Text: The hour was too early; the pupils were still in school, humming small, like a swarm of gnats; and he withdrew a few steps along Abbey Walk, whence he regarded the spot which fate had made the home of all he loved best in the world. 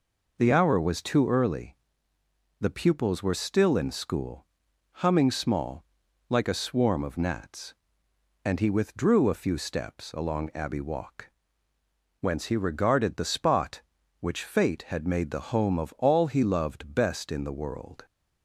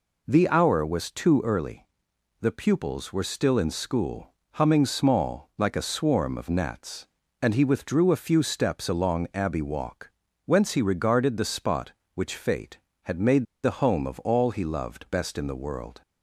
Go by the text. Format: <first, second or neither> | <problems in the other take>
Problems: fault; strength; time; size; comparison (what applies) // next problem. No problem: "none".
first | pauses between "made" and "the"; slight; at 13.4 s; 0.20 s long